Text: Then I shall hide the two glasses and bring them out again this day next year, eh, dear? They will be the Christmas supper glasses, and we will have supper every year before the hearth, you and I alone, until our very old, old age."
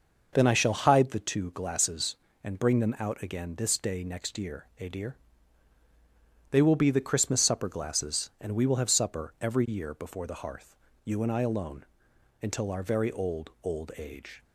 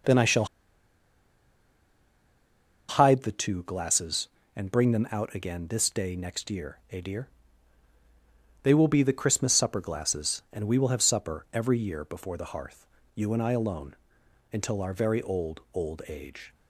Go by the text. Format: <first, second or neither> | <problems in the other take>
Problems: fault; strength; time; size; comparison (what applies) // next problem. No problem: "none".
first | pauses between "shall" and "hide"; strong; at 0.4 s; 2.4 s long